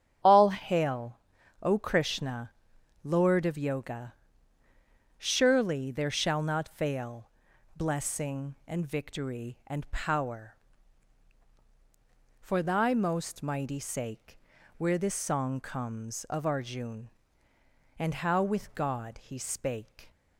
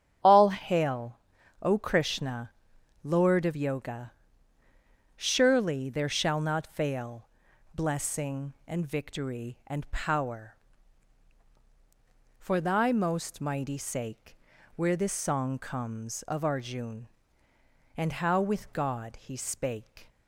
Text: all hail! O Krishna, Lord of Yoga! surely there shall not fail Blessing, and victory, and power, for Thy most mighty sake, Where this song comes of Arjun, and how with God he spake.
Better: neither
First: starts louder than the rest; strong; until 1.7 s; 8.5 dB // pauses between "fail" and "Blessing"; noticeable; at 7.2 s; 0.48 s long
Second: starts louder than the rest; strong; until 1.7 s; 8.5 dB // pauses between "fail" and "Blessing"; noticeable; at 7.2 s; 0.48 s long

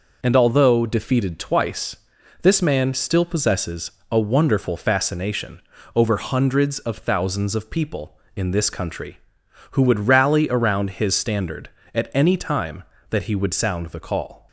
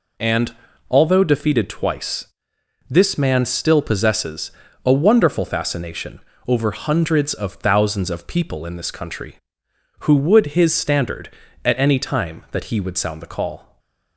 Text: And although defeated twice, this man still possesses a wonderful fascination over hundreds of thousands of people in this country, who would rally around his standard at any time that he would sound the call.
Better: first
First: pauses between "possesses" and "a"; slight; at 3.9 s; 0.20 s long // pauses between "fascination" and "over"; slight; at 5.6 s; 0.34 s long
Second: pauses between "And" and "although"; slight; at 0.5 s; 0.36 s long // pauses between "possesses" and "a"; slight; at 4.5 s; 0.34 s long // pauses between "fascination" and "over"; slight; at 6.2 s; 0.26 s long // skips "rally around"; at 10.4 s // stays silent after the last word; slight; from 13.6 s on; 0.5 s long

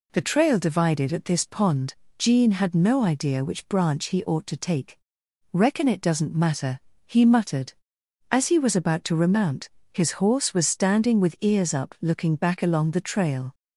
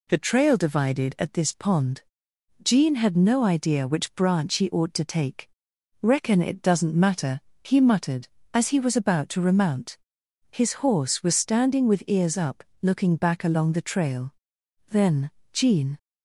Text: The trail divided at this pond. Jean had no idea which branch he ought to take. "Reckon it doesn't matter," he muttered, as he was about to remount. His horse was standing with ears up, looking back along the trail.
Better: first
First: none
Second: goes on to say "Then Jean"; noticeable; from 14.8 s on; 1.0 s long

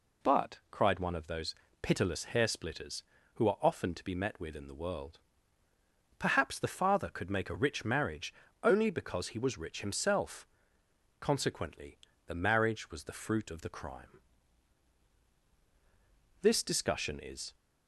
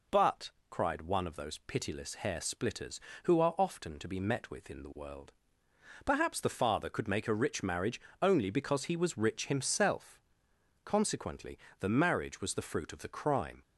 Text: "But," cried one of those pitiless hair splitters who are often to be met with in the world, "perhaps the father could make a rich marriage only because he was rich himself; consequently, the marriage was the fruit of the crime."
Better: second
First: pauses between "those" and "pitiless"; slight; at 1.5 s; 0.26 s long // pauses between "marriage" and "only"; slight; at 8.3 s; 0.28 s long // goes on to say "This discussion is"; noticeable; from 16.4 s on; 1.1 s long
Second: pauses between "marriage" and "only"; slight; at 8.0 s; 0.18 s long

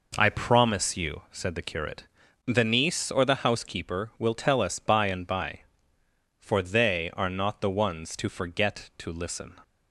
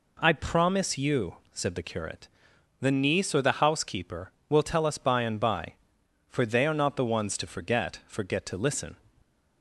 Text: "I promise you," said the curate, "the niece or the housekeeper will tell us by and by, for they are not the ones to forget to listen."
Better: first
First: none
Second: says "forget" twice; at 8.0 s

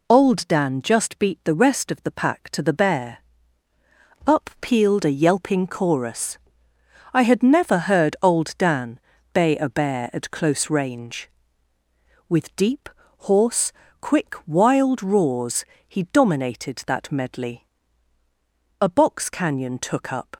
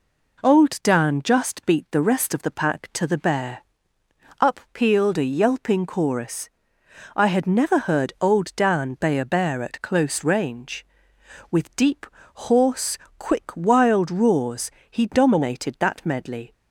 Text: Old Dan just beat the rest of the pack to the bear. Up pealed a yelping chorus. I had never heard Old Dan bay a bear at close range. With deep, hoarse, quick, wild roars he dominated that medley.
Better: second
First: pauses between "Dan" and "bay"; slight; at 8.9 s; 0.34 s long // pauses between "roars" and "he"; slight; at 15.6 s; 0.24 s long // goes on to say "A box canyon took up"; from 18.8 s on; 1.5 s long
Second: pauses between "roars" and "he"; slight; at 14.7 s; 0.18 s long

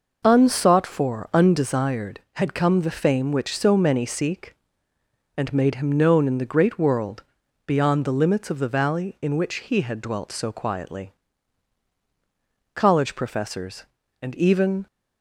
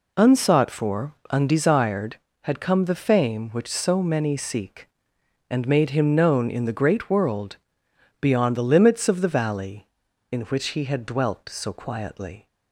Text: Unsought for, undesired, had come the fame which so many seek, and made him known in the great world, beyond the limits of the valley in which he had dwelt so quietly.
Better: second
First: goes on to say "College professors and even"; strong; from 12.8 s on; 2.0 s long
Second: none

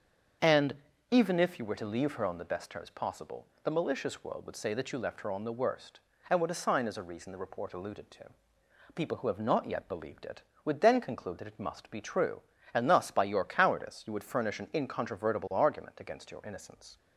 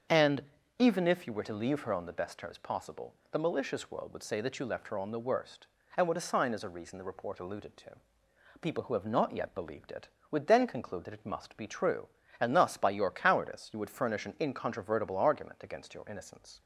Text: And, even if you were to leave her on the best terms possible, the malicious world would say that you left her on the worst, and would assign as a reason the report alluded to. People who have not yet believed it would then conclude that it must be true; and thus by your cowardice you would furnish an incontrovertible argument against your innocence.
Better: neither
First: starts louder than the rest; until 1.7 s; 6.5 dB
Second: starts louder than the rest; until 1.4 s; 6.5 dB

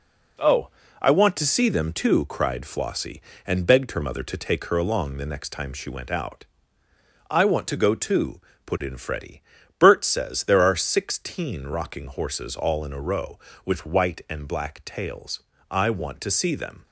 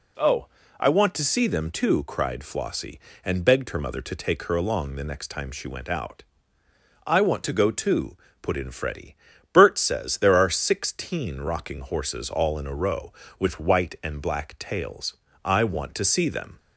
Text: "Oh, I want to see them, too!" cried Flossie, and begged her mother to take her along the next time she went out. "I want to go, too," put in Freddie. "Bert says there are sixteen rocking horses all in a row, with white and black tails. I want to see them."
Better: second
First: gets quieter; noticeable; throughout; 6 dB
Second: none

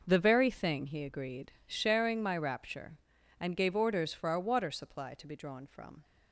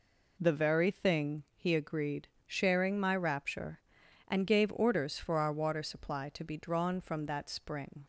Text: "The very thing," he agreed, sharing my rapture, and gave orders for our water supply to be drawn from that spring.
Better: second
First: stops before "that spring"; at 6.0 s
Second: none

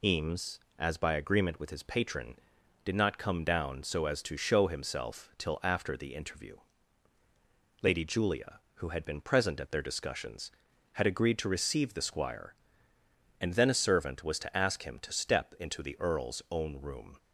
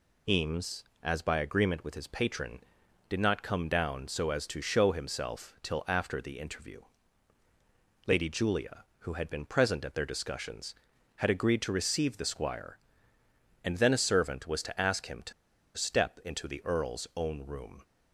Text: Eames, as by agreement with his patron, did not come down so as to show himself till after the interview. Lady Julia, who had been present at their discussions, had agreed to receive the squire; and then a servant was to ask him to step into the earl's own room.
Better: first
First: none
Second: pauses between "to" and "step"; at 15.3 s; 0.44 s long

